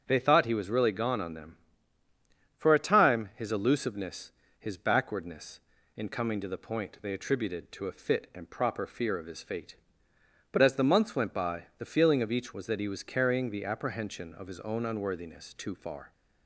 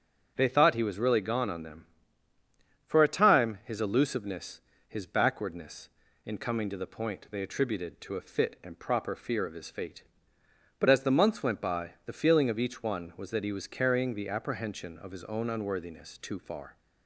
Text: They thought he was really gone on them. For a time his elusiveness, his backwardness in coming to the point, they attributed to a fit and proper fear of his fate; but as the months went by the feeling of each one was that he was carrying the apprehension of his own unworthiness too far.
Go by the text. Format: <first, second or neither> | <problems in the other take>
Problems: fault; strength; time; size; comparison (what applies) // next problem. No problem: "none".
second | starts louder than the rest; strong; until 1.0 s; 7.5 dB; also in the second // skips "one"; at 12.5 s